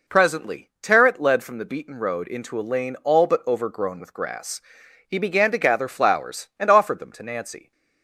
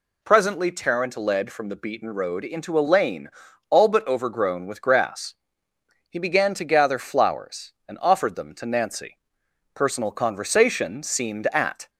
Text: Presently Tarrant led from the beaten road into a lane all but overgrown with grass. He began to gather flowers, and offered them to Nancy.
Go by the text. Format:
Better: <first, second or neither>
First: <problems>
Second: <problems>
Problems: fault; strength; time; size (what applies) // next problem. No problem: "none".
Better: first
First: none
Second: pauses between "lane" and "all"; at 3.2 s; 0.40 s long // goes on to say "Personal conversation seemed at"; strong; from 9.7 s on; 2.1 s long